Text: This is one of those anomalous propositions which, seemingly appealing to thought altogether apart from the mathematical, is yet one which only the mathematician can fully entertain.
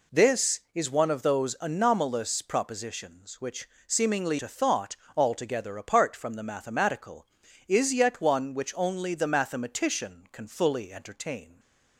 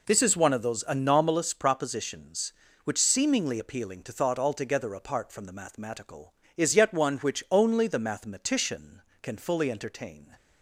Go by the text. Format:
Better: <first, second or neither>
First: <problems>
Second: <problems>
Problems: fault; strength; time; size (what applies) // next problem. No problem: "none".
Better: second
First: skips "appealing"; at 4.3 s // pauses between "thought" and "altogether"; slight; at 4.9 s; 0.18 s long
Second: none